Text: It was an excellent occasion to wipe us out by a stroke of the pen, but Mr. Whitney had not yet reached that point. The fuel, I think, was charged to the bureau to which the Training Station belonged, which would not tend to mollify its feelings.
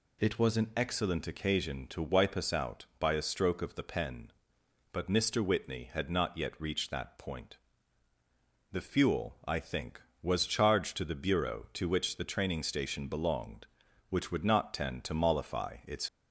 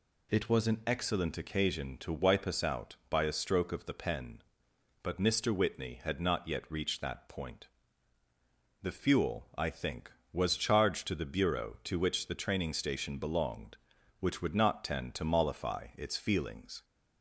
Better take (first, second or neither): second